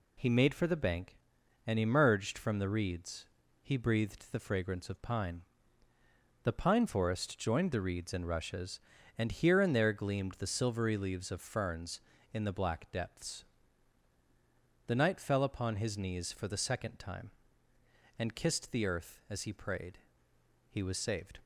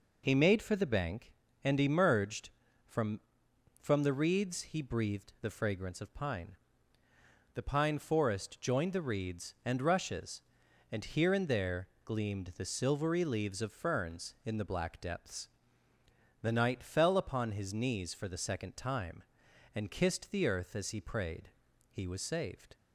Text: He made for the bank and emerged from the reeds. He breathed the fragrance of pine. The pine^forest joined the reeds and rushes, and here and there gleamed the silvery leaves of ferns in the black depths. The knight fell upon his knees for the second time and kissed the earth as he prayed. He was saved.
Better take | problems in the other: first | says "from" twice; at 3.7 s // pauses between "there" and "gleamed"; slight; at 11.8 s; 0.18 s long

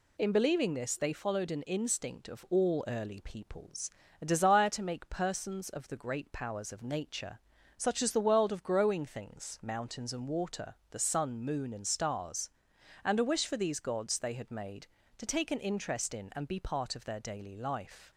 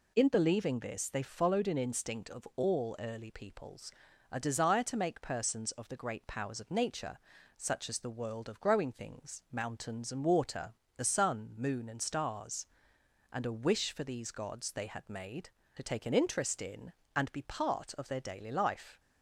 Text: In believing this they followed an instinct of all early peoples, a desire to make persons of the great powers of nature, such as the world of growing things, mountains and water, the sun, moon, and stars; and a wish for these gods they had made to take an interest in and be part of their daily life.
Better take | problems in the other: neither | none

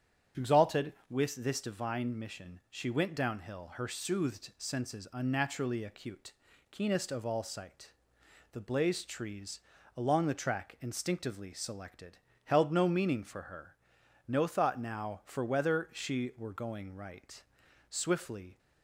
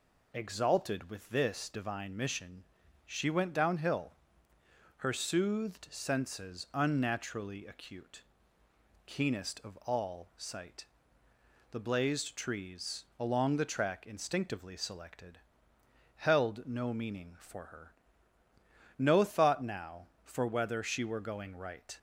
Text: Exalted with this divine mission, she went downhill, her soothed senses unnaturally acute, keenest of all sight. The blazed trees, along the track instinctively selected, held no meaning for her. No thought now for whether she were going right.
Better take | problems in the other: second | starts louder than the rest; strong; until 1.5 s; 7.5 dB // goes on to say "Swiftly"; noticeable; from 17.8 s on; 0.70 s long

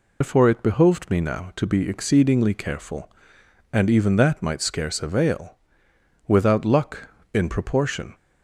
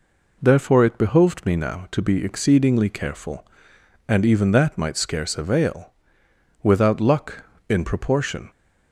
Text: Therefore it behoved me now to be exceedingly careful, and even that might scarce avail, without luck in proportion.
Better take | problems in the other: second | loses the start of "Therefore"; at 0.2 s; 160 ms

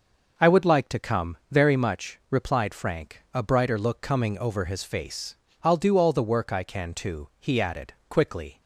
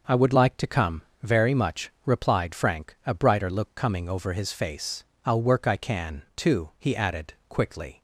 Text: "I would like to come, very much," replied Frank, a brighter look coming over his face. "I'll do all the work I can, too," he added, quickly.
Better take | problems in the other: first | skips "do all the"; at 5.4 s

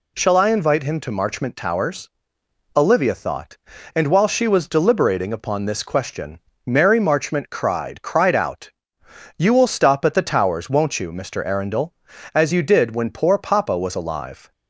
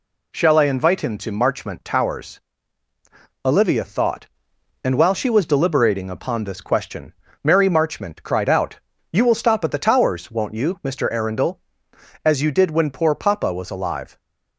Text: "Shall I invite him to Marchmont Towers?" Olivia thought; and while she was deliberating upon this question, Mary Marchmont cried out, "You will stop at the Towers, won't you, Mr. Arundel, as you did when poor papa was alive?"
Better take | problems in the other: second | says "cried" twice; at 8.0 s

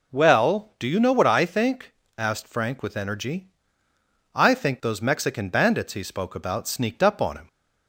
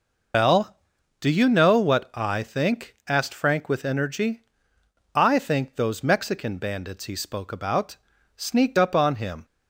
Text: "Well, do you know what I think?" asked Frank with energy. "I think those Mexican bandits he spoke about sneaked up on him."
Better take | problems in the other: first | loses the start of "Well"; at 0.3 s; 100 ms // pauses between "about" and "sneaked"; at 7.9 s; 0.40 s long

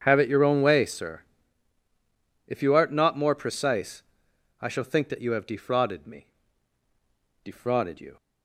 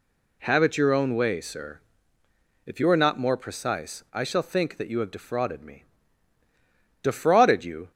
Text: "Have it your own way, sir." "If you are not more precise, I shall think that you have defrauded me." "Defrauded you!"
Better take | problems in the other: second | starts louder than the rest; strong; until 1.0 s; 7.5 dB // says "art" for "are"; at 2.7 s

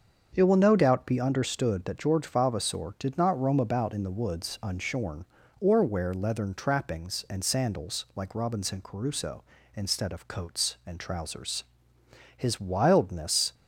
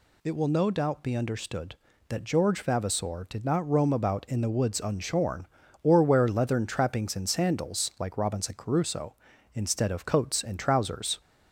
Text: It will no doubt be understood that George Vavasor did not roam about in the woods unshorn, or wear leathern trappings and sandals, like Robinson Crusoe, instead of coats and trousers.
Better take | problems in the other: second | starts louder than the rest; until 1.3 s; 7 dB // goes on to say "His wildness"; noticeable; from 12.3 s on; 1.1 s long

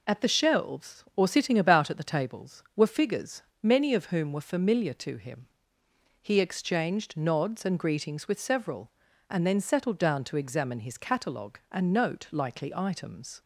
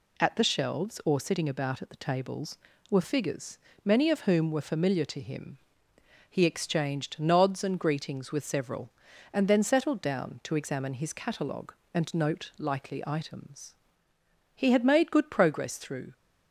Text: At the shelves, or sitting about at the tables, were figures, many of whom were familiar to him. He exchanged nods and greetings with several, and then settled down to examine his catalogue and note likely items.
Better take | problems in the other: first | goes on to say "He had made good progress through"; from 14.5 s on; 1.5 s long

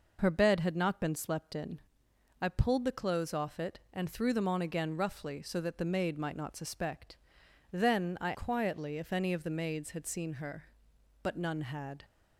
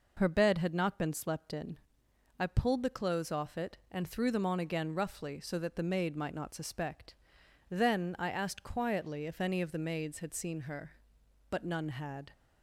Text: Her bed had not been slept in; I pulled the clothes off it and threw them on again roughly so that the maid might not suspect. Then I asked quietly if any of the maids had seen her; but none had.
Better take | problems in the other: second | skips "asked"; at 8.3 s

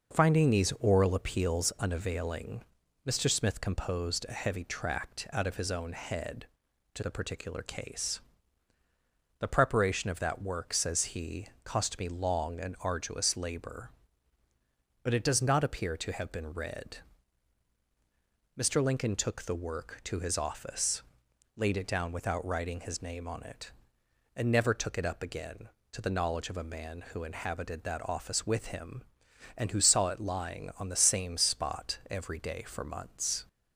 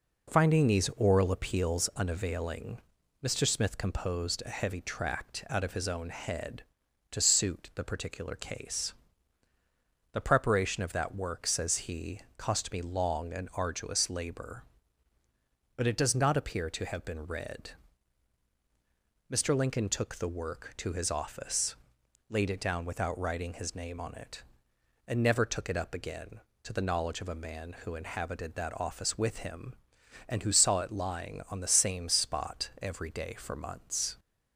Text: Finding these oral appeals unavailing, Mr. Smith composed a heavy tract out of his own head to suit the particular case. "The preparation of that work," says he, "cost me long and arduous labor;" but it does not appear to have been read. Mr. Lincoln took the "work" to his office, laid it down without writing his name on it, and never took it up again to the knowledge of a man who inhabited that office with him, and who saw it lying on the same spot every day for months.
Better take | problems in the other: second | skips "suit"; at 7.0 s

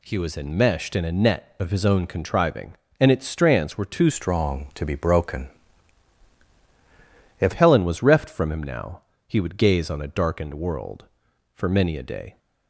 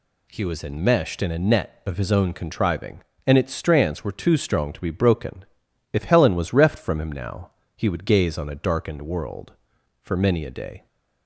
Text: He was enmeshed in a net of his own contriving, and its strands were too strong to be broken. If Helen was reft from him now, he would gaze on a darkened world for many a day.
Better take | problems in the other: second | changes voice from "strong" to "If"; from 4.0 to 7.5 s; 3.5 s long

